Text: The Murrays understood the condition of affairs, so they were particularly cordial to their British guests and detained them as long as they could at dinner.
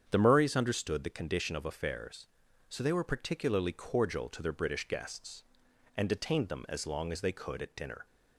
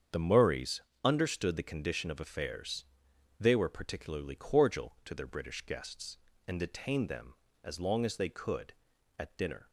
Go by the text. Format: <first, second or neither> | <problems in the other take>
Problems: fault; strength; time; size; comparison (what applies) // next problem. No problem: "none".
first | starts louder than the rest; strong; until 1.3 s; 7.5 dB; strong in the first // pauses between "Murrays" and "understood"; slight; at 0.8 s; 0.22 s long // skips "so"; at 3.1 s